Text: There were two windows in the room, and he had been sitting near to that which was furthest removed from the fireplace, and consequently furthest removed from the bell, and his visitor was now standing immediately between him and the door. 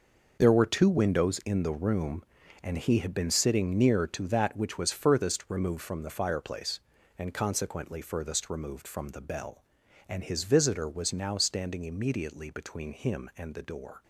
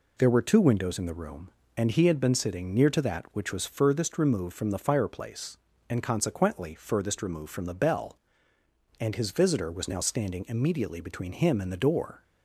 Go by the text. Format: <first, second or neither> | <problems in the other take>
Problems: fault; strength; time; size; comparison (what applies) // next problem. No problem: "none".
second | gets quieter; strong; throughout; 11 dB